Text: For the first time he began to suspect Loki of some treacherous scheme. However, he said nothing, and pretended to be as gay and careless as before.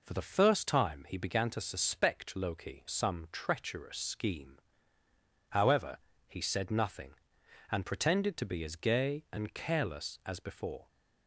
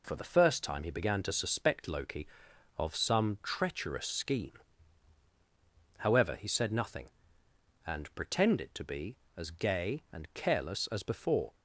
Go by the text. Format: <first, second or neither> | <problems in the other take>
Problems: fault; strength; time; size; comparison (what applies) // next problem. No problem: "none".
second | skips "of"; at 2.8 s